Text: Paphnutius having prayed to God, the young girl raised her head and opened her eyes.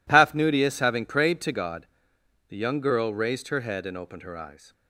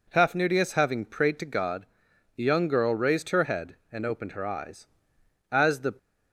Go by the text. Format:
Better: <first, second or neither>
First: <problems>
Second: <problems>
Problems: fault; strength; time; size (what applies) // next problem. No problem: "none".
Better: first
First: none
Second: goes on to say "As the"; slight; from 5.5 s on; 0.44 s long